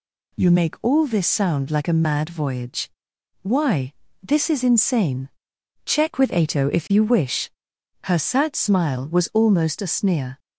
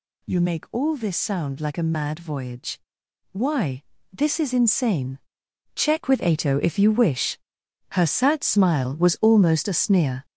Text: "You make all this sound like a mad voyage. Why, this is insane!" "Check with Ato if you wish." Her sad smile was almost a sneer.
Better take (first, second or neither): first